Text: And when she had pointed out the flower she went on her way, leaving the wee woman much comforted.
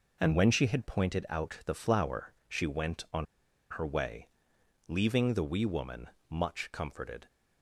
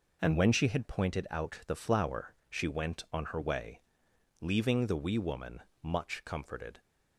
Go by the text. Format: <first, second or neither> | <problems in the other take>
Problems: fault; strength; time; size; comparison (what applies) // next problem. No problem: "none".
second | pauses between "flower" and "she"; slight; at 2.3 s; 0.16 s long; slight in the second // pauses between "on" and "her"; noticeable; at 3.2 s; 0.46 s long // pauses between "woman" and "much"; slight; at 6.0 s; 0.22 s long; slight in the second